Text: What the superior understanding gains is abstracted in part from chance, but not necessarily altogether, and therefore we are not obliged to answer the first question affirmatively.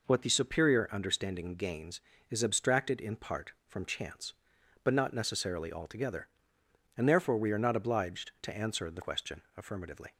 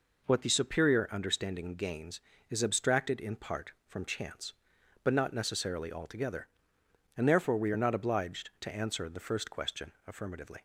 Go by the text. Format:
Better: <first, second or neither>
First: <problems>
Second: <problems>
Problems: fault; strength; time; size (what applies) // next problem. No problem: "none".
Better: second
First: skips "first"; at 9.0 s // pauses between "question" and "affirmatively"; slight; at 9.4 s; 0.16 s long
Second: pauses between "question" and "affirmatively"; slight; at 9.9 s; 0.16 s long